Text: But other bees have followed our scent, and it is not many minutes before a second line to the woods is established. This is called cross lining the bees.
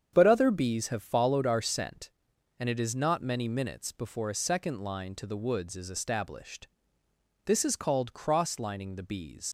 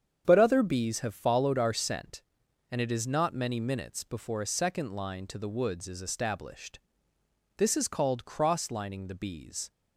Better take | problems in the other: second | starts louder than the rest; strong; until 1.1 s; 8 dB; strong in the second // leaves "bees" unfinished; at 9.4 s; 65 ms

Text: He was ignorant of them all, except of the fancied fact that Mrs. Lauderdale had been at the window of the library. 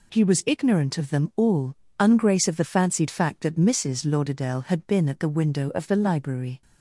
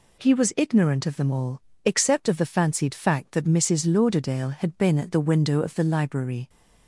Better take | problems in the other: second | says "ungrace" for "except"; at 1.9 s

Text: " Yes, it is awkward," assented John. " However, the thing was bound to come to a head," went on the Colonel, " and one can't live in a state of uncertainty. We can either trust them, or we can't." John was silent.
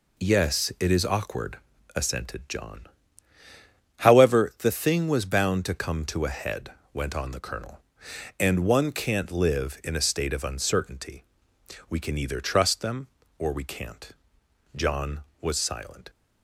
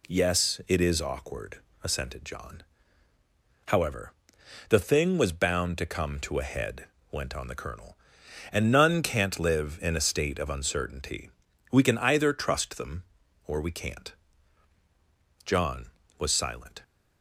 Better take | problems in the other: first | says "none" for "one"; at 8.7 s

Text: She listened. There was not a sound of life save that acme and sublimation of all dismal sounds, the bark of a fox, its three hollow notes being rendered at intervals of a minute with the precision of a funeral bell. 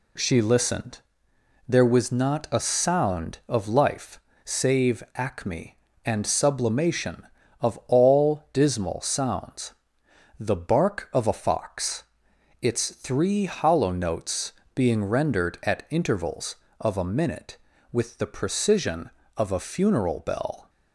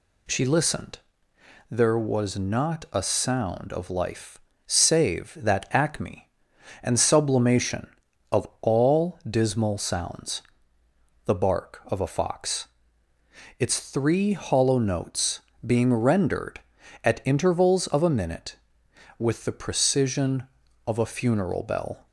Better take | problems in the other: second | pauses between "life" and "save"; slight; at 4.1 s; 0.26 s long; slight in the second // skips "that"; at 5.0 s // pauses between "notes" and "being"; slight; at 14.5 s; 0.22 s long; slight in the second

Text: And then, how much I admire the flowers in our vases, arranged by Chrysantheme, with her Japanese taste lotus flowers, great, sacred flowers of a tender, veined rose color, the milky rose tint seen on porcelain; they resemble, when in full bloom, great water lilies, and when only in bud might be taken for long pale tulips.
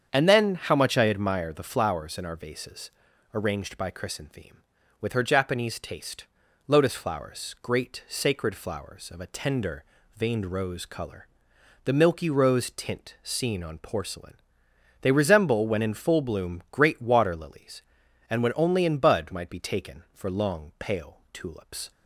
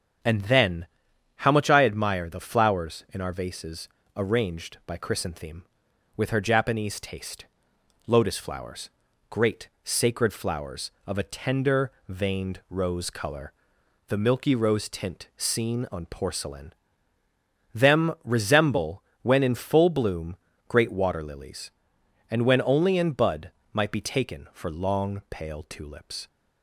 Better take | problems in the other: first | starts louder than the rest; strong; until 1.7 s; 7.5 dB; strong in the first // pauses between "taste" and "lotus"; noticeable; at 7.4 s; 0.62 s long; also in the first // says "them" for "they"; at 17.7 s // pauses between "bud" and "might"; slight; at 23.5 s; 0.22 s long

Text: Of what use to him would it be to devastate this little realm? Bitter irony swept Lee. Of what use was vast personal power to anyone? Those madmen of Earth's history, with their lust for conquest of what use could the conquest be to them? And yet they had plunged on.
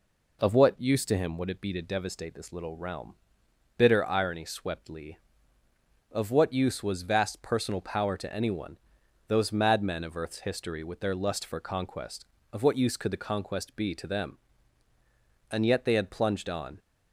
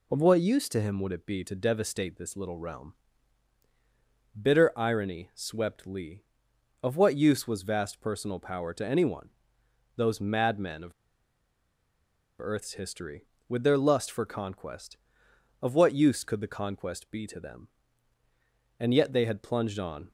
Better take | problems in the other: first | pauses between "of" and "Earth's"; strong; at 10.9 s; 1.4 s long

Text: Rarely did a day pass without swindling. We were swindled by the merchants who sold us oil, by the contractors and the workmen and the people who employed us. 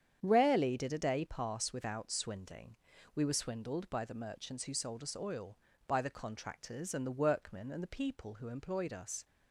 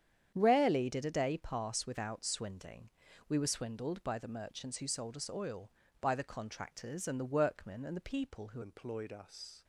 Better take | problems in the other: first | starts louder than the rest; strong; until 1.3 s; 8.5 dB; strong in the first // changes voice at "employed"; from 8.6 s on; 1.0 s long

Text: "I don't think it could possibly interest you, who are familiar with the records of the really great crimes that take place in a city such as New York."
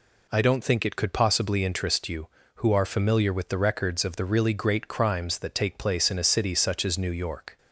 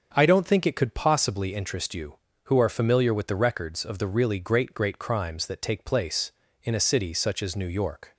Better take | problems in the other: first | starts louder than the rest; until 1.1 s; 6.5 dB // says "great" twice; at 4.7 s

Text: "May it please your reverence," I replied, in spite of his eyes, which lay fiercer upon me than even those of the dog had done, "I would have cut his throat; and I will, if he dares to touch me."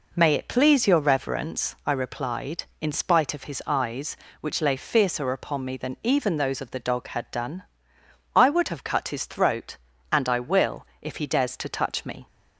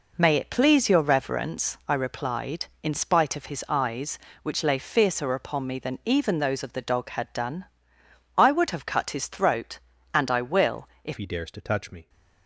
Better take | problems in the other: first | changes voice at "he"; from 11.1 s on; 0.9 s long

